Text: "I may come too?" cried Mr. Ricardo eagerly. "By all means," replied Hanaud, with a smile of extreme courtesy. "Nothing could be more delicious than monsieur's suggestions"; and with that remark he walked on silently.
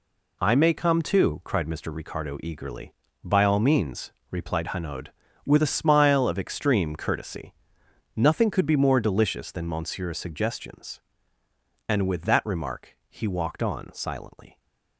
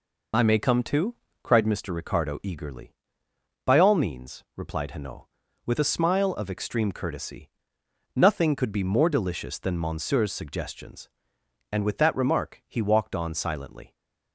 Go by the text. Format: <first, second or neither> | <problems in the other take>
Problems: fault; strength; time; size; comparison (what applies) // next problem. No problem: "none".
neither | none